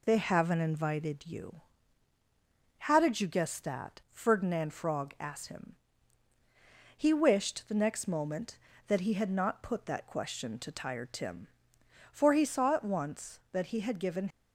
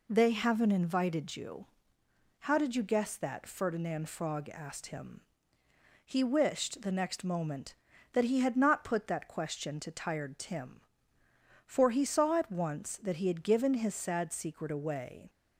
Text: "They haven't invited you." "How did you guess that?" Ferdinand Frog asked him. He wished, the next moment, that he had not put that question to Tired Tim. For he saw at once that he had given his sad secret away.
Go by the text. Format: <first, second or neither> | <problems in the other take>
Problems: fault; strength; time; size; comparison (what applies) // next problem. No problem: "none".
second | stops before "his sad secret away"; at 14.3 s